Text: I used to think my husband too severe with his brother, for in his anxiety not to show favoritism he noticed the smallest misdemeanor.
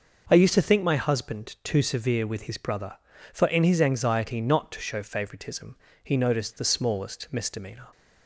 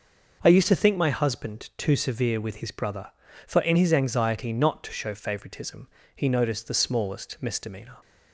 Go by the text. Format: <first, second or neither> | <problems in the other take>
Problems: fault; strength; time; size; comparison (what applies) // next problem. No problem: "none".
neither | pauses between "favoritism" and "he"; slight; the same in both